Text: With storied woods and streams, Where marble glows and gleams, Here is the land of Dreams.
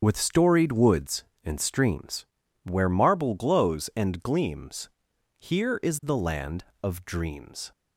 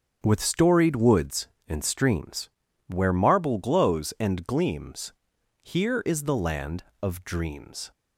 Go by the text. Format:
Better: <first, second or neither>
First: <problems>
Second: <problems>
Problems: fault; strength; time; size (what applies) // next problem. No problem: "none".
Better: second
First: loses the start of "With"; at 0.0 s; 25 ms // starts louder than the rest; strong; until 1.0 s; 7.5 dB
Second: starts louder than the rest; until 1.2 s; 7 dB